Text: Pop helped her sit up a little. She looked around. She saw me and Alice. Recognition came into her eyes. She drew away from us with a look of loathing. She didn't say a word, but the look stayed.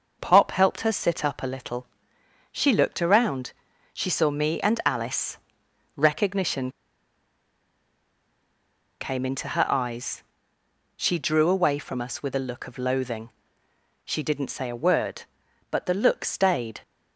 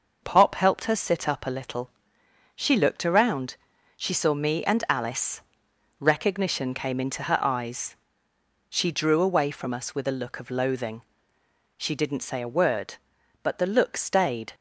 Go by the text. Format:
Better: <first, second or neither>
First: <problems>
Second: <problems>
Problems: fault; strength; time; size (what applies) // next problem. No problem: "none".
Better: second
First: pauses between "Recognition" and "came"; strong; at 6.6 s; 2.3 s long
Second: none